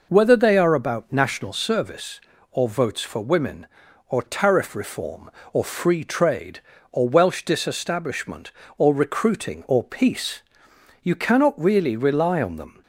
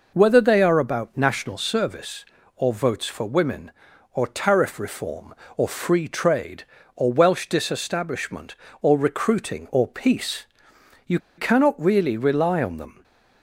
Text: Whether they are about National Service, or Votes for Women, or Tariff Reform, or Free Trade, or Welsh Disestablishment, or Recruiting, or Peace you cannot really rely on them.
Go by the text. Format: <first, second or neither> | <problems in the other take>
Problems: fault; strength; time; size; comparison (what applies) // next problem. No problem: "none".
first | pauses between "Peace" and "you"; noticeable; at 10.4 s; 0.60 s long; noticeable in the first // pauses between "you" and "cannot"; slight; at 11.1 s; 0.19 s long